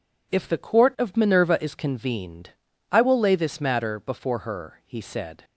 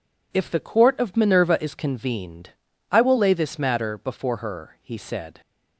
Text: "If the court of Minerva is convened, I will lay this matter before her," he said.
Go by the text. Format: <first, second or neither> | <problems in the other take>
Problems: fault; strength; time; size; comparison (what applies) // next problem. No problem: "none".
neither | none